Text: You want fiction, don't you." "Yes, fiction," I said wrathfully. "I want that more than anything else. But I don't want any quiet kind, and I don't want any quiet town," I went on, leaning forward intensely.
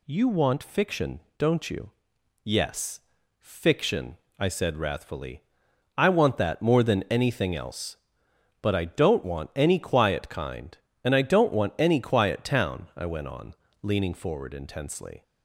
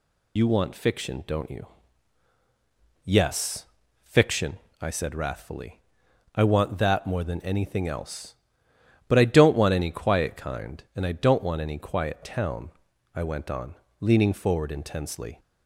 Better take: first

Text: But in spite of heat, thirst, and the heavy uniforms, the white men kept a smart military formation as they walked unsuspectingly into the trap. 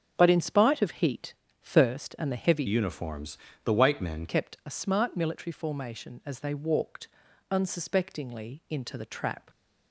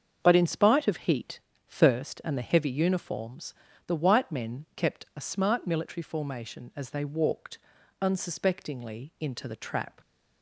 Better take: second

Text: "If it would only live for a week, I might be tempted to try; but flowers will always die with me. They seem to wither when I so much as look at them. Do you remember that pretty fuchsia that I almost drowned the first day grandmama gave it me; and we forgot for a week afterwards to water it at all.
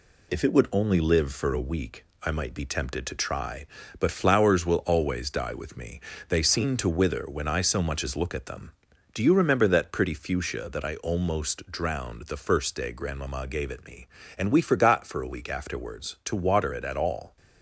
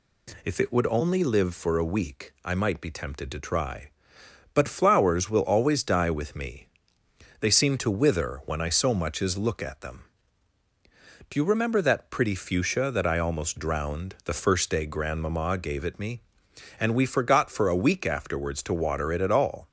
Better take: second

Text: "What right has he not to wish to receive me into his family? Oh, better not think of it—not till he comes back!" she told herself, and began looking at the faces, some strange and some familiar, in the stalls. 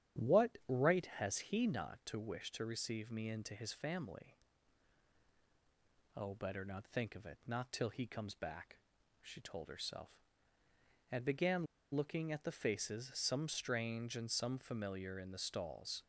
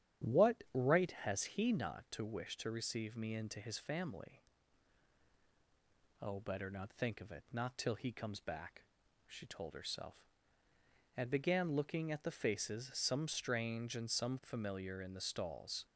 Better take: second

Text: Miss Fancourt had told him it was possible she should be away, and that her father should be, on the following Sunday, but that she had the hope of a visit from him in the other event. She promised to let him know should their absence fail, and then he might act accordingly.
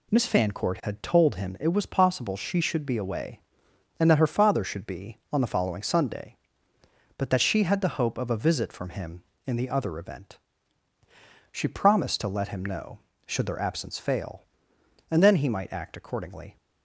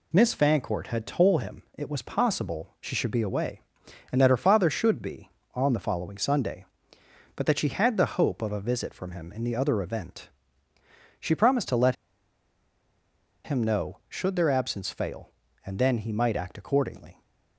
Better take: first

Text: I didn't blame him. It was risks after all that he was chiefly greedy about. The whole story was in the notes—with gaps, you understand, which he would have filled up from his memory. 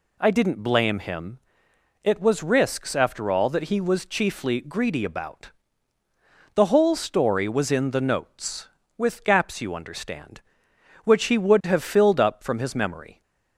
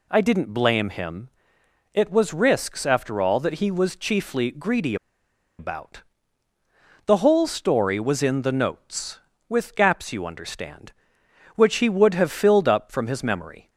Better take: first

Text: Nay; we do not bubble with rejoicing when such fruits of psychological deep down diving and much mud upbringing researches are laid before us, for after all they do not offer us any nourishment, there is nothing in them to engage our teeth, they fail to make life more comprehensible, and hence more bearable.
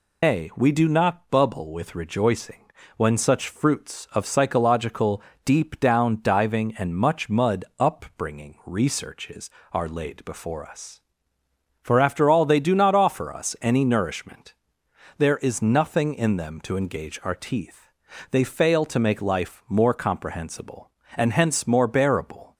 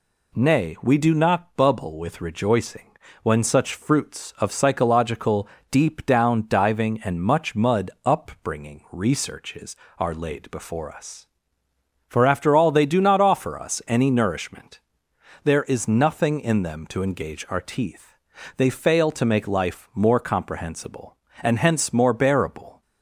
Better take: second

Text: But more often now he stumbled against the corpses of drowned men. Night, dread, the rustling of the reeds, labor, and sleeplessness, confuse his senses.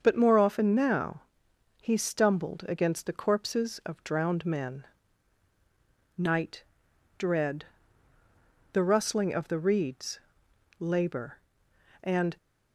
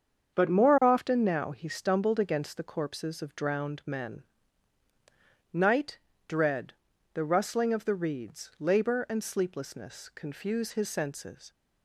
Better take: second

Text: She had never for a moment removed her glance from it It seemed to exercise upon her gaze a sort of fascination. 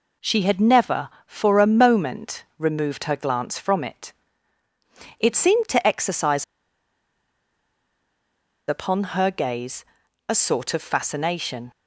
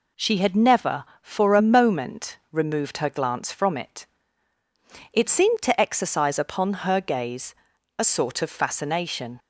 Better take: second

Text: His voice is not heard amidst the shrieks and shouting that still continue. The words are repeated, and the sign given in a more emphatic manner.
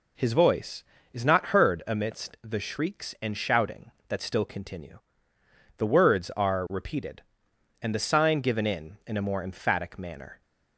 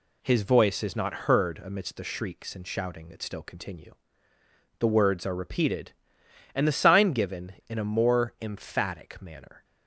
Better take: second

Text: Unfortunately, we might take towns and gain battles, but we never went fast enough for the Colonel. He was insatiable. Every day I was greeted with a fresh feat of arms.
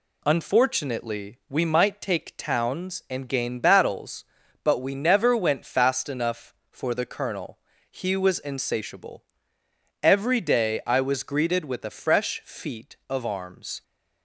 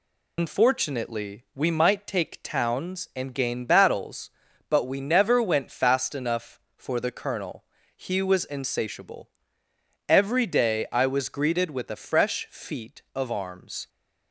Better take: first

